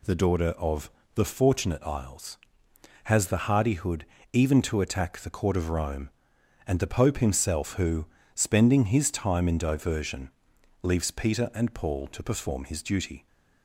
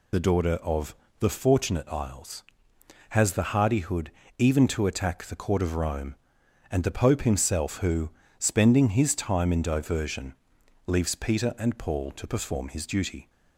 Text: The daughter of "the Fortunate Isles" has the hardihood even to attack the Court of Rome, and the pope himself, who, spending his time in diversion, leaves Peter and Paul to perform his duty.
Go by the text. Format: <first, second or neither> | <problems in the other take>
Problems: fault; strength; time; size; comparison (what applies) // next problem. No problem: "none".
first | loses the start of "The"; at 0.1 s; 50 ms // pauses between "of" and "the"; slight; at 0.9 s; 0.24 s long; slight in the first // pauses between "hardihood" and "even"; slight; at 4.0 s; 0.28 s long; slight in the first